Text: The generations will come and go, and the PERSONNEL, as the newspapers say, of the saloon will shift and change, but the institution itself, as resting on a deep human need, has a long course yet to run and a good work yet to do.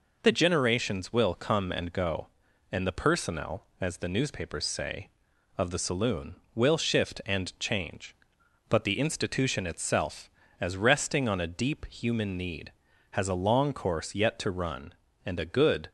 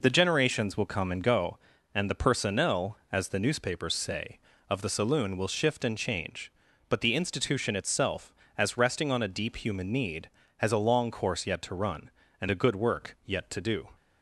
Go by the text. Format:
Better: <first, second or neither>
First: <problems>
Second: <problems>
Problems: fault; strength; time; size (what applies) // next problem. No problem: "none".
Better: second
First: stops before "work yet to do"; at 15.8 s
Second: none